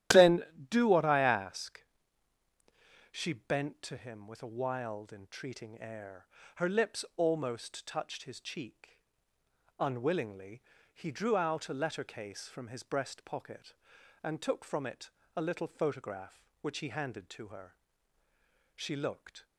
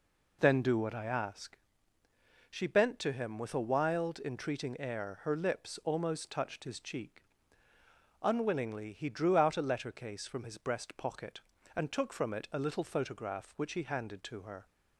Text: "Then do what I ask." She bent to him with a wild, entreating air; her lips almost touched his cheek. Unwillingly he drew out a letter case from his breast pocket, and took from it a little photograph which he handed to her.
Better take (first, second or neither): second